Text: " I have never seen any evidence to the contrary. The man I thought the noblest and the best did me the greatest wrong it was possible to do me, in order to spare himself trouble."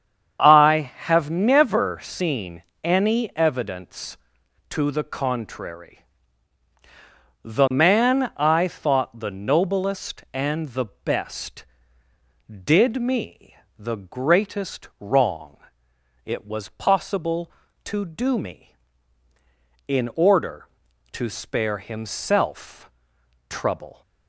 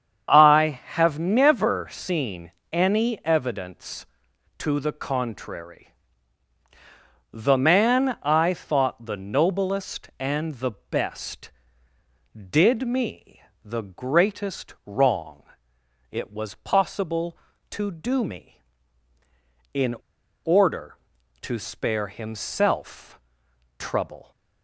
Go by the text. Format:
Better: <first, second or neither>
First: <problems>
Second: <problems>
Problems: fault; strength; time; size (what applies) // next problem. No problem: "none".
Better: first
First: starts louder than the rest; strong; until 1.4 s; 8 dB // pauses between "seen" and "any"; slight; at 2.6 s; 0.20 s long // pauses between "me" and "the"; slight; at 13.5 s; 0.24 s long // pauses between "wrong" and "it"; noticeable; at 15.5 s; 0.66 s long // pauses between "himself" and "trouble"; noticeable; at 22.8 s; 0.58 s long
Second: starts louder than the rest; strong; until 1.3 s; 8 dB // pauses between "seen" and "any"; slight; at 2.5 s; 0.20 s long // pauses between "me" and "the"; slight; at 13.4 s; 0.24 s long // pauses between "wrong" and "it"; noticeable; at 15.4 s; 0.66 s long // pauses between "in" and "order"; noticeable; at 19.9 s; 0.49 s long // pauses between "himself" and "trouble"; noticeable; at 23.1 s; 0.58 s long